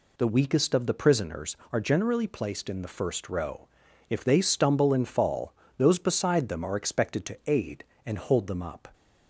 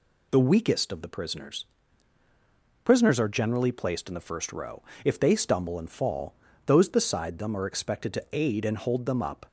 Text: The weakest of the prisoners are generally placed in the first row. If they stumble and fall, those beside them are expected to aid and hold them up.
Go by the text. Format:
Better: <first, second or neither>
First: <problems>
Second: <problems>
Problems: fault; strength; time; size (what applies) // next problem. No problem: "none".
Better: first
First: none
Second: says "prisoners" twice; at 2.8 s